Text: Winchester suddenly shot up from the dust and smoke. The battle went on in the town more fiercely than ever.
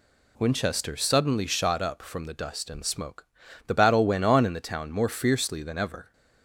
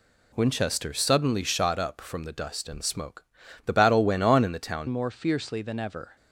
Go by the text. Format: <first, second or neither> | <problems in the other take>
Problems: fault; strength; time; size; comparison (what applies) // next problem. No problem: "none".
first | changes voice at "more"; from 4.8 s on; 1.3 s long